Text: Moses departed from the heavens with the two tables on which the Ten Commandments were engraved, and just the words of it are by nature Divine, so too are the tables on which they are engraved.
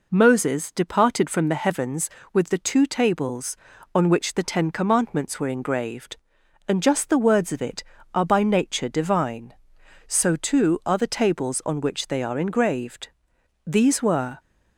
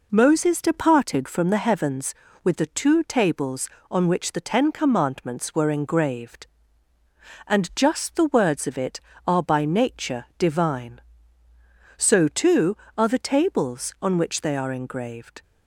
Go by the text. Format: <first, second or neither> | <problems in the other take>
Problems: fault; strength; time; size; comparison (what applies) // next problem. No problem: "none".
second | goes on to say "These were"; noticeable; from 13.6 s on; 0.76 s long